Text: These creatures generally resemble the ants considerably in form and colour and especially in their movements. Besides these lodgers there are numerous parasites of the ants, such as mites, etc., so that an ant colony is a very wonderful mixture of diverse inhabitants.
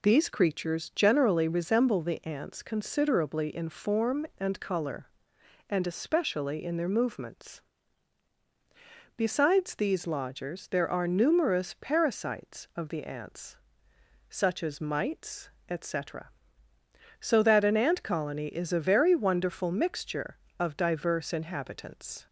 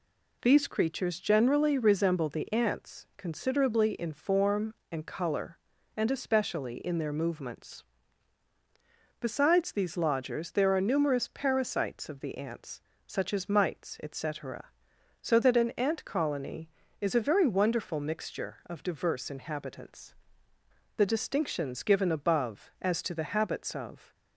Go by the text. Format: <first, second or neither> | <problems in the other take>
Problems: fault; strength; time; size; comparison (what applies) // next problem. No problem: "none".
first | goes on to say "The distinctions given above as to the habits of"; strong; from 20.9 s on; 3.1 s long